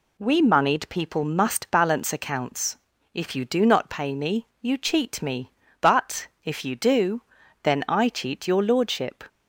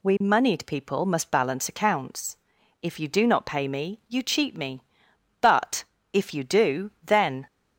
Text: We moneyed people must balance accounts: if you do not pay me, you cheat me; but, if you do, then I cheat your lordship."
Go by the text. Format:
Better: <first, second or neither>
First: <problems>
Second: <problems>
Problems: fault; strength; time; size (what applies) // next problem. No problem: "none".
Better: first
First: none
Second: stops before "I cheat your lordship"; at 7.4 s